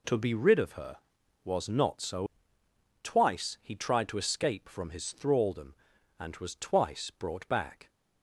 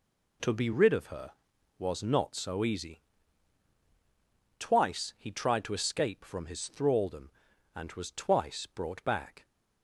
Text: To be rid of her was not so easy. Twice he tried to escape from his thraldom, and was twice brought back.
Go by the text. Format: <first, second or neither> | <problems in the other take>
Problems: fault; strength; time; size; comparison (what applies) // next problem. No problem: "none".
second | skips "easy"; at 2.6 s